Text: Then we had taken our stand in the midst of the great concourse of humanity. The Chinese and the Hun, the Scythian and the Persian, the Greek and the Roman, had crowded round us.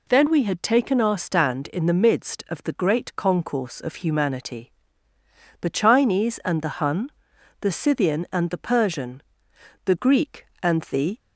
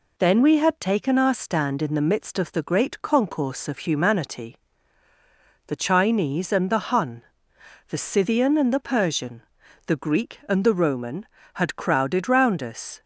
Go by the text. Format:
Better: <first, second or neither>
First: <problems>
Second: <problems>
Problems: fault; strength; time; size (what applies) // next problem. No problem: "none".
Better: second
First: stops before "Roman had crowded round us"; at 11.1 s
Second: none